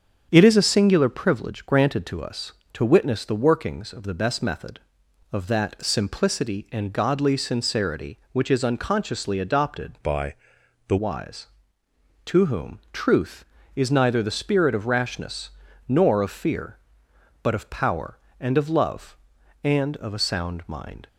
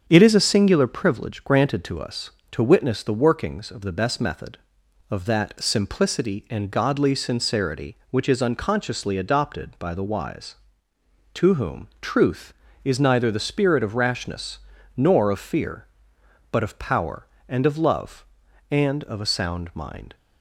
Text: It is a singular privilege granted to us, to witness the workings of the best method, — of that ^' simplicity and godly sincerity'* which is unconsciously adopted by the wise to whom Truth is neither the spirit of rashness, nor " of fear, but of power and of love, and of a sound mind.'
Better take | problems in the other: second | starts louder than the rest; strong; until 1.3 s; 7.5 dB; strong in the second // changes voice from "by" to "the"; from 10.0 to 10.9 s; 0.9 s long // pauses between "by" and "the"; noticeable; at 10.3 s; 0.54 s long

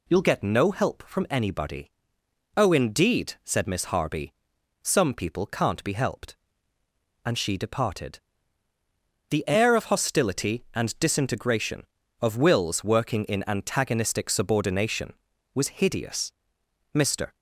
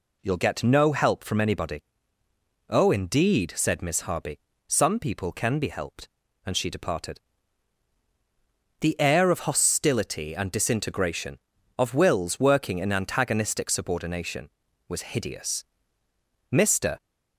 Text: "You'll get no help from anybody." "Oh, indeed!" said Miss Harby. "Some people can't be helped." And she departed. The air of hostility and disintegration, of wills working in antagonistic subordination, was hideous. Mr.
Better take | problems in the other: first | says "can" for "can't"; at 5.3 s

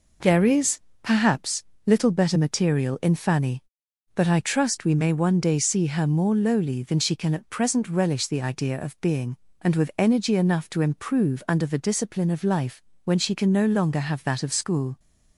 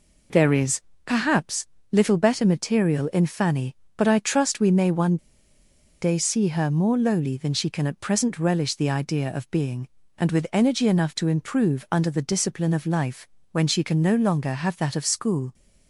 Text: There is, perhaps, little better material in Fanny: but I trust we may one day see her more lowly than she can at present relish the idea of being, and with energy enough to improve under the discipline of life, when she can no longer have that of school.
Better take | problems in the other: first | pauses between "one" and "day"; noticeable; at 5.1 s; 0.84 s long

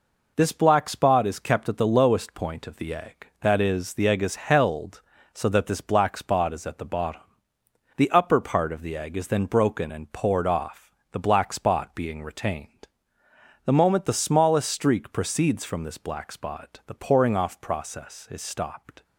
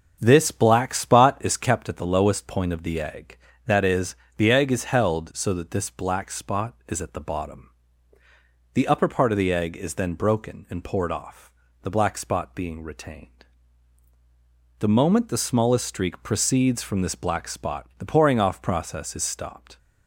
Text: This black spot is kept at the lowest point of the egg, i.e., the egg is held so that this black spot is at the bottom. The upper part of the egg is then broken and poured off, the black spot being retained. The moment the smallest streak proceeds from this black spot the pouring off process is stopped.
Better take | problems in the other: first | starts louder than the rest; until 1.9 s; 6.5 dB

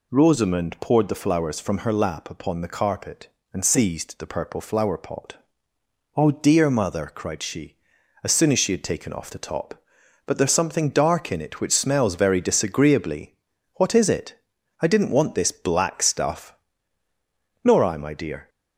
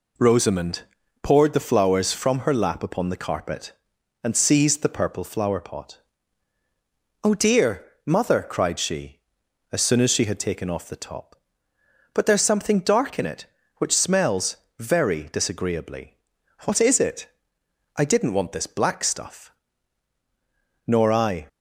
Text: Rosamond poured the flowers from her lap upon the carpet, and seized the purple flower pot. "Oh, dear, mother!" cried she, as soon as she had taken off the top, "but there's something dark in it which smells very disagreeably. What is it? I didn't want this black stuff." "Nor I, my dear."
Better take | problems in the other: first | pauses between "Rosamond" and "poured"; at 0.8 s; 0.38 s long // pauses between "smells" and "very"; slight; at 14.5 s; 0.22 s long // stops before "my dear"; at 21.4 s

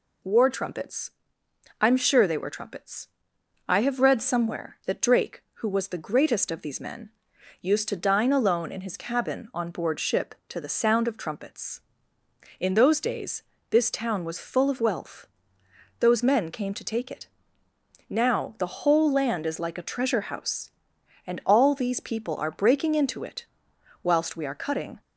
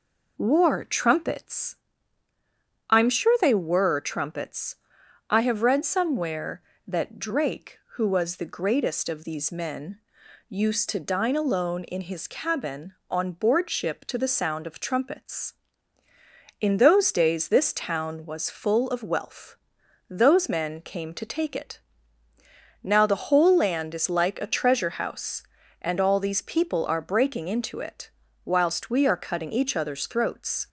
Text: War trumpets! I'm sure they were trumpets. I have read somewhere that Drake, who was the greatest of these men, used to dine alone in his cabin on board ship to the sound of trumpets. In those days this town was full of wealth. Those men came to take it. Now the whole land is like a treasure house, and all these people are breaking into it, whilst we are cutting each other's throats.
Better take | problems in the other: second | pauses between "days" and "this"; slight; at 13.4 s; 0.28 s long // stops before "each other's throats"; at 25.0 s

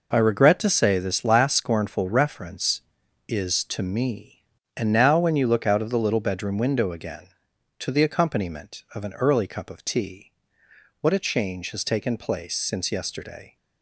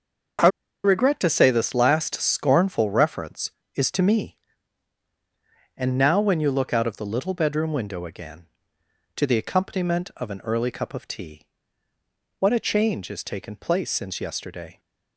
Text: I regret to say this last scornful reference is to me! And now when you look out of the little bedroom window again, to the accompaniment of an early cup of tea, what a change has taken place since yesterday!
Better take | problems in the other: first | starts louder than the rest; until 1.7 s; 6.5 dB // pauses between "I" and "regret"; at 0.4 s; 0.36 s long

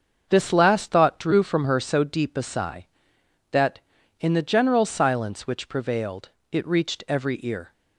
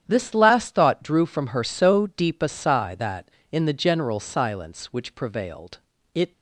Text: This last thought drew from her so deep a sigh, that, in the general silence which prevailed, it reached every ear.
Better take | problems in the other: first | starts louder than the rest; strong; until 1.0 s; 9.5 dB; also in the first // stops before "reached every ear"; at 6.3 s

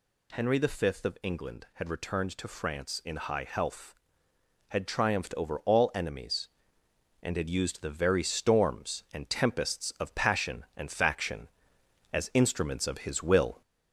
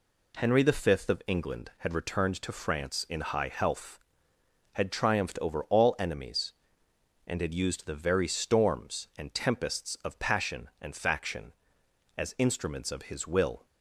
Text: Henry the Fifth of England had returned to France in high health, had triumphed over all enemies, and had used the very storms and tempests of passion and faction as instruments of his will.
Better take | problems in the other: second | gets louder; slight; throughout; 2.5 dB

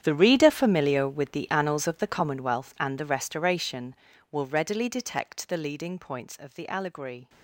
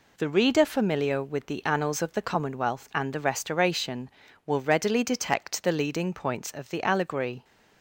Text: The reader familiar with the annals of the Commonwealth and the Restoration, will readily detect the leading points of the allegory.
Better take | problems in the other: second | gets quieter; strong; throughout; 16.5 dB

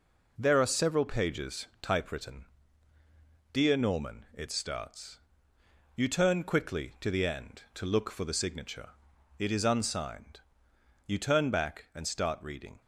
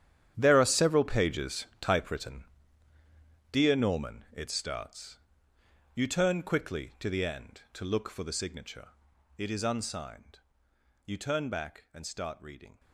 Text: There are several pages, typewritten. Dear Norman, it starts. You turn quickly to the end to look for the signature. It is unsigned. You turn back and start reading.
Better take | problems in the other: first | gets quieter; strong; throughout; 14.5 dB

